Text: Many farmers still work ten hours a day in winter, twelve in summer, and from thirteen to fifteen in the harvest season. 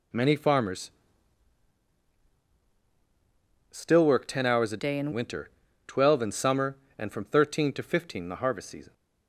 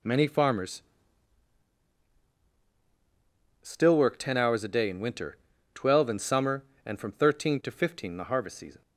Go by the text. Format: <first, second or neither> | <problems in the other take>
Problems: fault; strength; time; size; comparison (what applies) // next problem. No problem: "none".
second | pauses between "farmers" and "still"; strong; at 0.9 s; 2.8 s long; strong in the second // changes voice from "day" to "in"; from 4.7 to 5.1 s; 0.4 s long